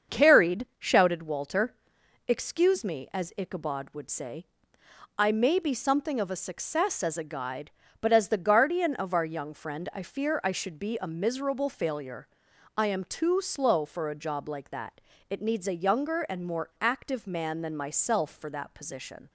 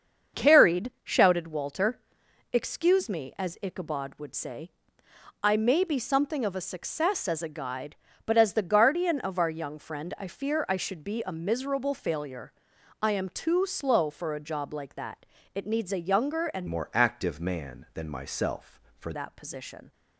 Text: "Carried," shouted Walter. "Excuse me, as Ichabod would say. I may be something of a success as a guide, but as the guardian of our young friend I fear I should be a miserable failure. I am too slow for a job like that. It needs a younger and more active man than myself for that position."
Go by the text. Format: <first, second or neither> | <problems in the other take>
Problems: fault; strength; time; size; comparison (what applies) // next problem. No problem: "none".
first | starts louder than the rest; until 1.4 s; 7 dB; also in the first // changes voice from "more" to "for"; from 16.6 to 19.1 s; 2.5 s long